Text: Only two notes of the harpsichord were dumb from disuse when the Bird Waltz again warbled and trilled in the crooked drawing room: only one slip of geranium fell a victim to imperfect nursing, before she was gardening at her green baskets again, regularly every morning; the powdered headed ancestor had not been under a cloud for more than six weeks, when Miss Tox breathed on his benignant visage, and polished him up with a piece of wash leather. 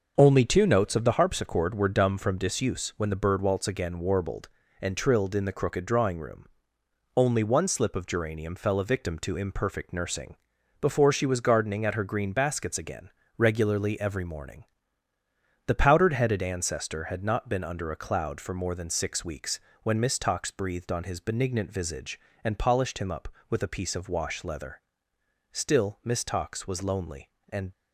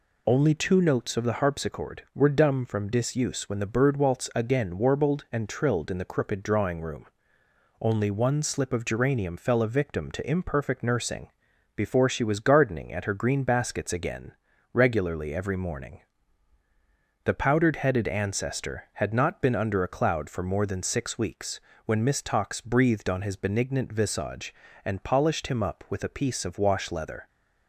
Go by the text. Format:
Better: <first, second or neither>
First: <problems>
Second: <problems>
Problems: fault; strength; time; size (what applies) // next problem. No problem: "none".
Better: second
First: goes on to say "Still Miss Tox was lonely and"; strong; from 25.5 s on; 2.1 s long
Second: none